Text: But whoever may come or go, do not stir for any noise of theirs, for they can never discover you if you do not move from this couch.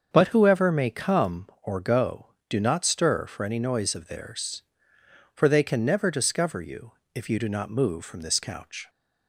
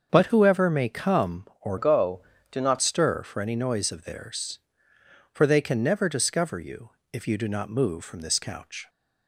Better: first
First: starts louder than the rest; until 1.1 s; 6.5 dB // pauses between "you" and "if"; slight; at 6.9 s; 0.24 s long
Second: starts louder than the rest; until 1.1 s; 6.5 dB // changes voice from "go" to "not"; from 1.7 to 2.7 s; 1.0 s long // pauses between "you" and "if"; slight; at 6.8 s; 0.24 s long

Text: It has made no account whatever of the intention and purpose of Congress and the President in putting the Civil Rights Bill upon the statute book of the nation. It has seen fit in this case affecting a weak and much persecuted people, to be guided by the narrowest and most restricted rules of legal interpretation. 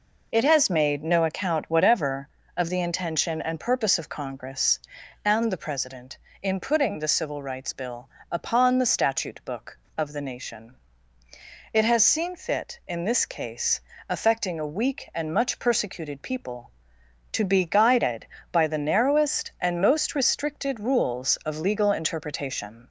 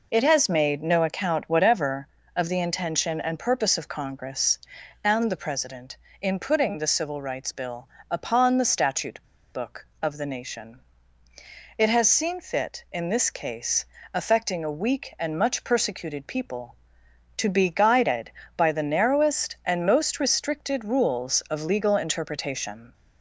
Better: first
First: pauses between "Bill" and "upon"; slight; at 8.0 s; 0.22 s long // pauses between "case" and "affecting"; slight; at 13.7 s; 0.28 s long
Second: pauses between "Bill" and "upon"; slight; at 7.8 s; 0.22 s long // pauses between "statute" and "book"; slight; at 9.2 s; 0.30 s long // pauses between "case" and "affecting"; slight; at 13.8 s; 0.28 s long

